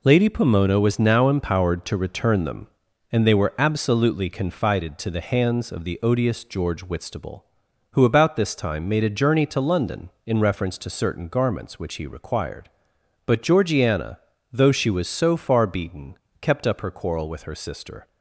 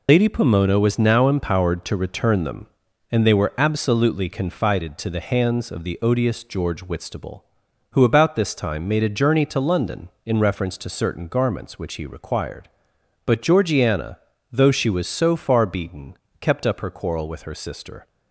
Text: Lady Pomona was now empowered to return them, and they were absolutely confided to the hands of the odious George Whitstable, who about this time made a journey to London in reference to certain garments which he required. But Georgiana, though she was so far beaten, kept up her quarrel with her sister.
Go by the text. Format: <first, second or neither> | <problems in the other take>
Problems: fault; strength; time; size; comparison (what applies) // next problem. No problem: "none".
first | loses the start of "Lady"; at 0.0 s; 55 ms